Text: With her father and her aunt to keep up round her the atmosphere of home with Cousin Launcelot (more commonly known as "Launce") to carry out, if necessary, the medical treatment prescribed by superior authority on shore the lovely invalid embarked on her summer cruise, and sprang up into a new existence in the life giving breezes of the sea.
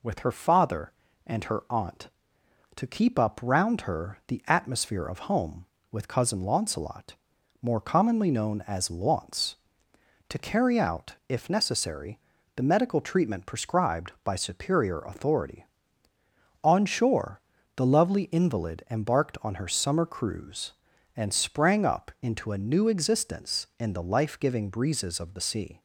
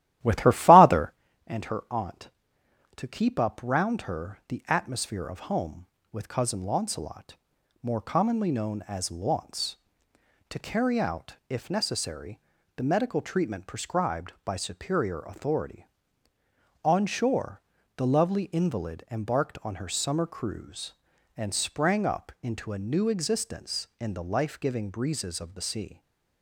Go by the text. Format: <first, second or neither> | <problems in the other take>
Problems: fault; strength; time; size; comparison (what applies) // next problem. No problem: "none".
first | starts louder than the rest; strong; until 1.1 s; 13.5 dB // pauses between "shore" and "the"; slight; at 17.6 s; 0.34 s long; slight in the first